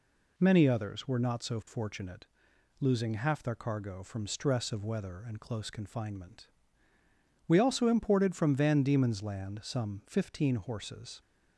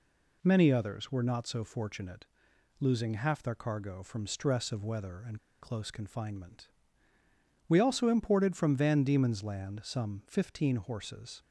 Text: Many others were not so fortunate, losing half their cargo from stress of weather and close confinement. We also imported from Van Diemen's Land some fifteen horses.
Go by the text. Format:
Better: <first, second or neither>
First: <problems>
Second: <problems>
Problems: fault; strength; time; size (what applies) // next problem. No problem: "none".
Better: first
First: none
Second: pauses between "and" and "close"; slight; at 5.3 s; 0.22 s long